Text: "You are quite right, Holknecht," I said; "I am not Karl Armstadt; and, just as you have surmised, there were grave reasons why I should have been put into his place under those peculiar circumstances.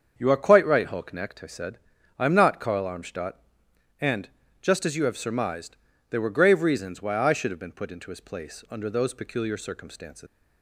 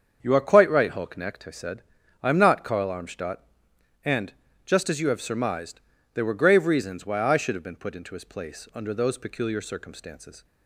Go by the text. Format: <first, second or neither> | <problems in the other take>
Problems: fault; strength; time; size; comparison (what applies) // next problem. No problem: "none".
second | starts louder than the rest; until 1.1 s; 7 dB; also in the second // leaves "circumstances" unfinished; at 10.2 s; 135 ms